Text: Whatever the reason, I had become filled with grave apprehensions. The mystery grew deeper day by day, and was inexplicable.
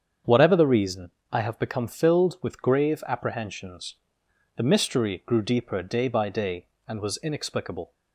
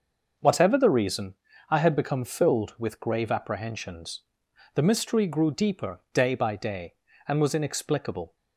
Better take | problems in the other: second | starts louder than the rest; strong; until 1.4 s; 7.5 dB; also in the second // says "have" for "had"; at 1.4 s

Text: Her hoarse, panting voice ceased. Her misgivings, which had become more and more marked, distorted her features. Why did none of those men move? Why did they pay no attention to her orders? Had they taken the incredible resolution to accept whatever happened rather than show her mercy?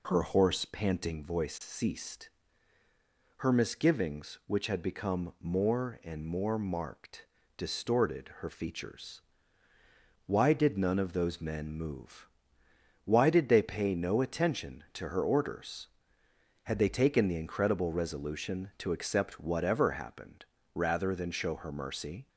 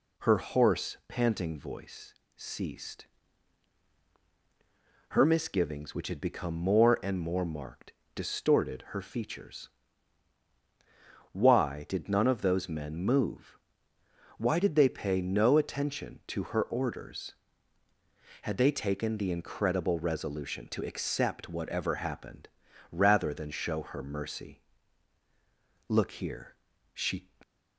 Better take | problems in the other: first | pauses between "voice" and "ceased"; slight; at 2.1 s; 0.22 s long // pauses between "happened" and "rather"; at 22.4 s; 0.42 s long; slight in the first // goes on to say "Look here she"; from 25.8 s on; 1.4 s long

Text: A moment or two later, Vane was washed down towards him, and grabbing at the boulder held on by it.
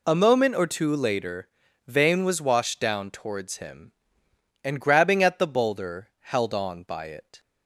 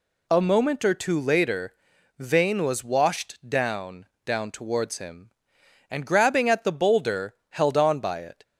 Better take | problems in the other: first | says "down" twice; at 4.2 s // pauses between "boulder" and "held"; slight; at 7.3 s; 0.16 s long

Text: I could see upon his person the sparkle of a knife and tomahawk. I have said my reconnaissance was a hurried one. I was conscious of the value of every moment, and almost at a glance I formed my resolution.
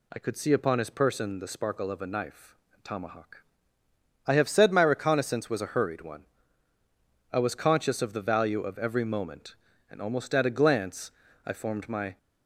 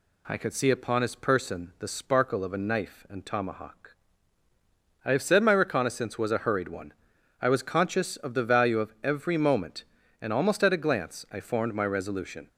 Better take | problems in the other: second | pauses between "glance" and "I"; slight; at 11.1 s; 0.34 s long // stops before "resolution"; at 12.1 s

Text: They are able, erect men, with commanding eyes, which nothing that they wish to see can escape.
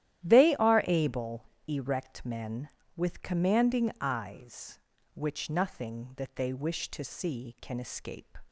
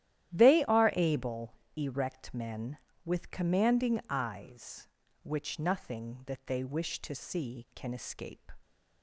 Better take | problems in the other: neither | starts louder than the rest; strong; the same in both

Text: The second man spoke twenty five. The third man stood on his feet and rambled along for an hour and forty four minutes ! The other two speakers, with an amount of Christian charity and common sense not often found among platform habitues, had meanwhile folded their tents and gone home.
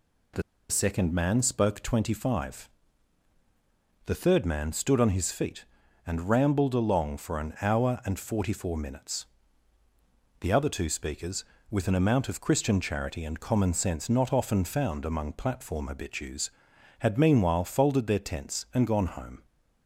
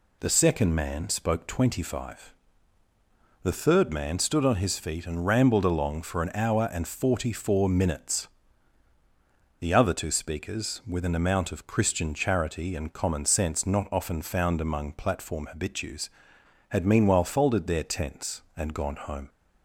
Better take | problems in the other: second | pauses between "The" and "second"; slight; at 0.4 s; 0.27 s long

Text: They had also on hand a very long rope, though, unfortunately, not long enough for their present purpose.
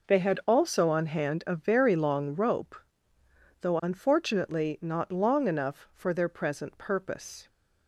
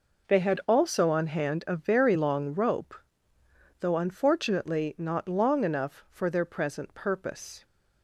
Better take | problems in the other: neither | none

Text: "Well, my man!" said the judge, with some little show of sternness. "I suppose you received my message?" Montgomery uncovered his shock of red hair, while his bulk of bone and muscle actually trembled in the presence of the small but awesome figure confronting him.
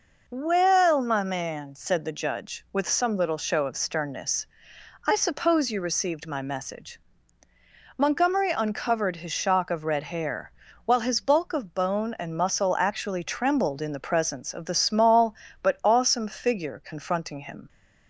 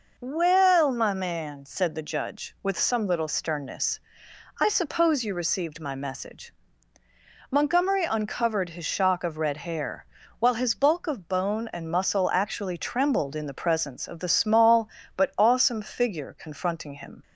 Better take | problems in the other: first | skips "show of"; at 3.2 s

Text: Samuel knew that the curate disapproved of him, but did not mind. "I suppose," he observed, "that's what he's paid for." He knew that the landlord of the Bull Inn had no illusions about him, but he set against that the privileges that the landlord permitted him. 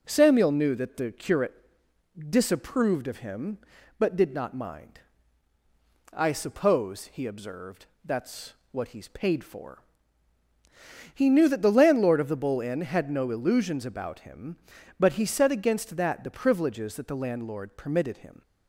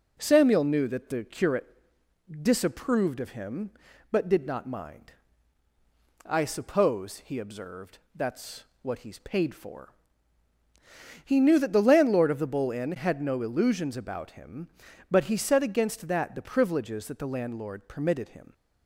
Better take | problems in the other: neither | pauses between "curate" and "disapproved"; noticeable; the same in both // pauses between "that's" and "what"; slight; the same in both

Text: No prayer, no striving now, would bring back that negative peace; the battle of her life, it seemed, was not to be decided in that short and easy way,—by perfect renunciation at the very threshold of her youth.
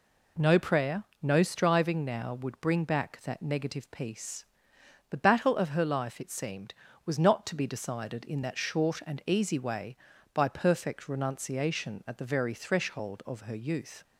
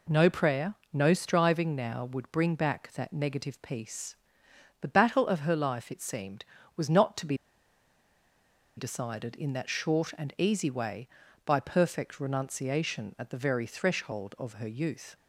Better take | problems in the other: first | pauses between "be" and "decided"; strong; at 7.3 s; 1.4 s long

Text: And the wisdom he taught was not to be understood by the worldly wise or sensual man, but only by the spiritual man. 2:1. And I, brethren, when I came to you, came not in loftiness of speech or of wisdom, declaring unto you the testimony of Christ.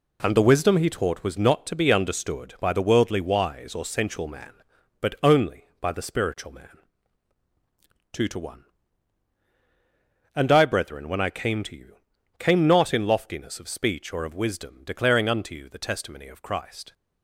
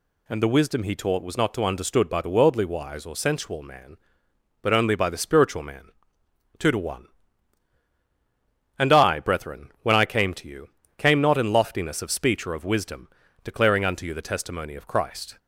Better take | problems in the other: first | skips "be"; at 1.6 s

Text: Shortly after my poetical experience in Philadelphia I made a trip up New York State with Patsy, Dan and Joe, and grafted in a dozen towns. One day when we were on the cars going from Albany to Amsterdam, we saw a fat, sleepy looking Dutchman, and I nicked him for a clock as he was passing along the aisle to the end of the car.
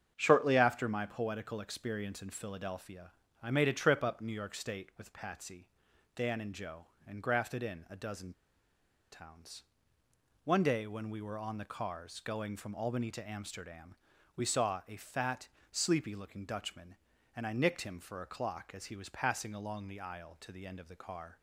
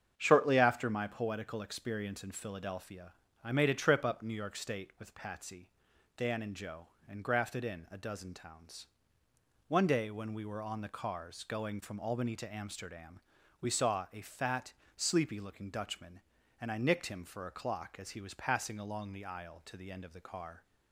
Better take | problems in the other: second | starts louder than the rest; strong; until 1.1 s; 7.5 dB; strong in the second // pauses between "Philadelphia" and "I"; slight; at 3.0 s; 0.32 s long; slight in the second // pauses between "dozen" and "towns"; noticeable; at 8.3 s; 0.80 s long

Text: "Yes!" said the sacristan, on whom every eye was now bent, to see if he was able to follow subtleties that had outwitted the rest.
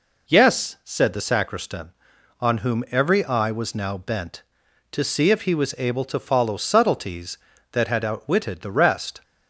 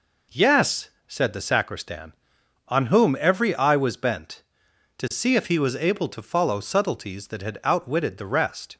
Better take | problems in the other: first | skips "now"; at 3.9 s

